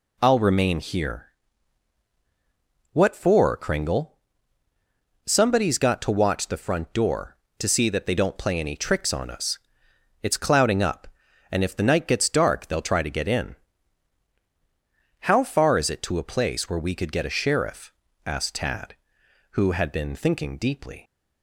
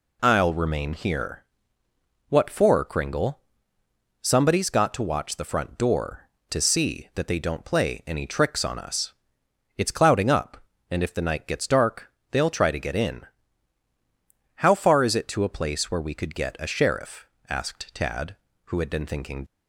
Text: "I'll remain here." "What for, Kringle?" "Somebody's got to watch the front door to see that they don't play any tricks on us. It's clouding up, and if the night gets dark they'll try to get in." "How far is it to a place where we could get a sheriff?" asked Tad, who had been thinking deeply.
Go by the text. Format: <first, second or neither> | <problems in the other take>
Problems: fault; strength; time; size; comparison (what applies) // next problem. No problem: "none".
first | pauses between "dark" and "they'll"; slight; at 12.1 s; 0.20 s long // stops before "deeply"; at 19.4 s